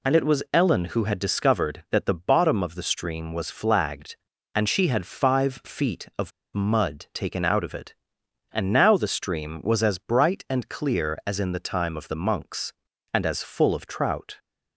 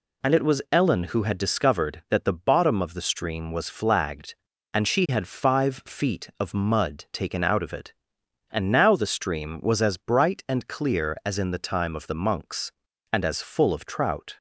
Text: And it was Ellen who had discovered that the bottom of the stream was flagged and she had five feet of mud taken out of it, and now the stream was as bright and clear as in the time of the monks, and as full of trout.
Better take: second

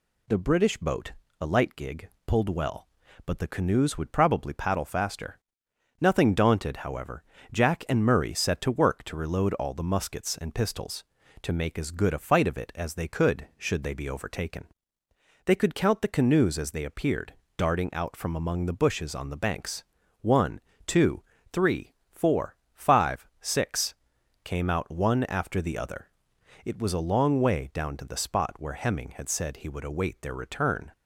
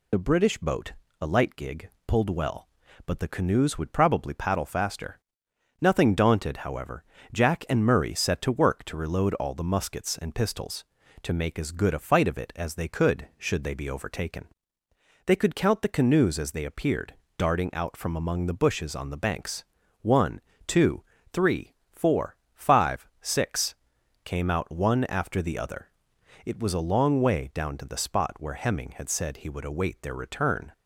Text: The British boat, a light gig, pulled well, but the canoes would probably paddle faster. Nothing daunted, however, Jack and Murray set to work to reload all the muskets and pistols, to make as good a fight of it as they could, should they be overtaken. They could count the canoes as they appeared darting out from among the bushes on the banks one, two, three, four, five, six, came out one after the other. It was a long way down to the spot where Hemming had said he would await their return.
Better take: first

